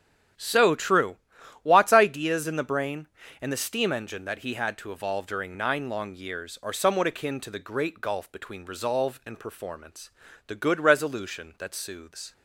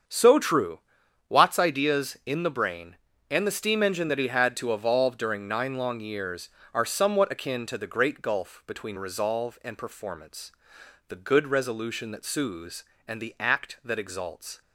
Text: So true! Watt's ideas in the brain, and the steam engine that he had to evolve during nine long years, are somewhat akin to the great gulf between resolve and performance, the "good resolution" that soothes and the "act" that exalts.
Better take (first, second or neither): second